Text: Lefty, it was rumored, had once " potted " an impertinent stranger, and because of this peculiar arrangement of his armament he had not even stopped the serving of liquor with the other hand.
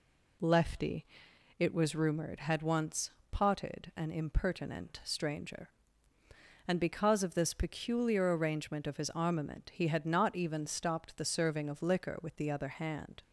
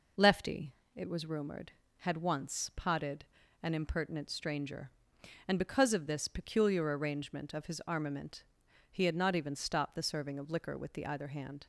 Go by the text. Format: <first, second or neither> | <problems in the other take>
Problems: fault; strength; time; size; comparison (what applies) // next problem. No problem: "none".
first | pauses between "armament" and "he"; noticeable; at 8.4 s; 0.46 s long // says "either" for "other"; at 11.0 s